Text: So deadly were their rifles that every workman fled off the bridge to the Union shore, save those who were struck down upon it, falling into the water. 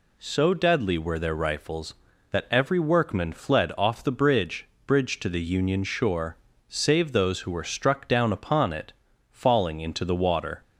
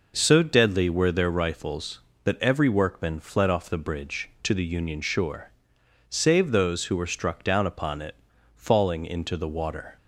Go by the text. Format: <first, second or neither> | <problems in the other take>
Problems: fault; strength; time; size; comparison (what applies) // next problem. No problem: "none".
second | says "bridge" twice; at 4.8 s